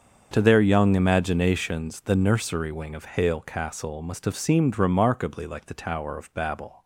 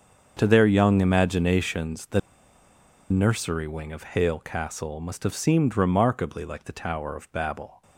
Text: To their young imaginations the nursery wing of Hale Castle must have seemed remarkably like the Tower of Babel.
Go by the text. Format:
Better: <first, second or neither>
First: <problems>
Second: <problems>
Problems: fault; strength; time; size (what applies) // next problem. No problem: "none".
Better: first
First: starts louder than the rest; until 1.3 s; 7 dB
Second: starts louder than the rest; until 1.3 s; 7 dB // pauses between "the" and "nursery"; noticeable; at 2.1 s; 0.91 s long